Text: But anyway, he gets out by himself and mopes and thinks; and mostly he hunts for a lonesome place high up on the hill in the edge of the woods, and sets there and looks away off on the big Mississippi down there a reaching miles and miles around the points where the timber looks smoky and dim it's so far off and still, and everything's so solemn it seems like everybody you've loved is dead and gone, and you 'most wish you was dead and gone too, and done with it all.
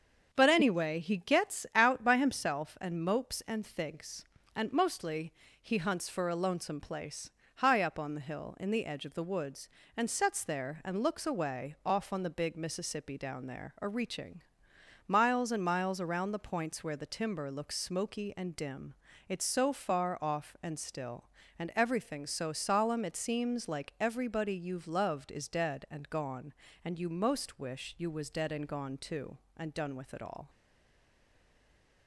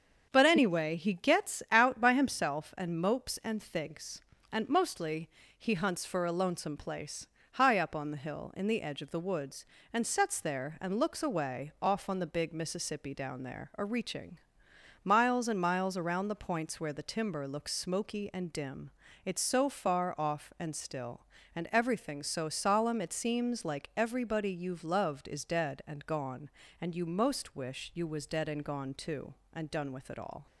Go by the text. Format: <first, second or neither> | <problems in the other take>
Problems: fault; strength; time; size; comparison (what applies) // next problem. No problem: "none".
second | starts louder than the rest; until 1.3 s; 6.5 dB; also in the second // pauses between "mostly" and "he"; slight; at 5.3 s; 0.28 s long; slight in the second // pauses between "place" and "high"; slight; at 7.2 s; 0.26 s long; slight in the second // pauses between "reaching" and "miles"; noticeable; at 14.4 s; 0.64 s long; noticeable in the second // pauses between "dim" and "it's"; slight; at 18.9 s; 0.34 s long; slight in the second // stays silent after the last word; noticeable; from 30.4 s on; 1.6 s long